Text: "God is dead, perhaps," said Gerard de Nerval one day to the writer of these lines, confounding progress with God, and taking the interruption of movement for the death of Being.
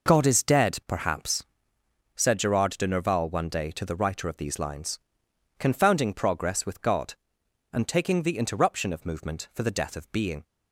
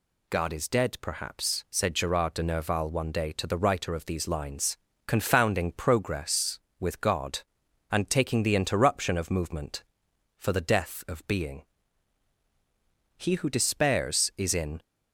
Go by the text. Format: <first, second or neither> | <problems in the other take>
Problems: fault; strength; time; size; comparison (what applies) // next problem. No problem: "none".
first | goes on to say "He who despairs is in"; from 13.1 s on; 1.6 s long